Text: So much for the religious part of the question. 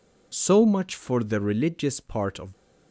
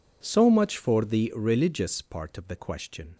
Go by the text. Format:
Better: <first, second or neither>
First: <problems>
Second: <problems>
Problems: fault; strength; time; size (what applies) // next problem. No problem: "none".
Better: second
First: stops before "the question"; at 2.5 s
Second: none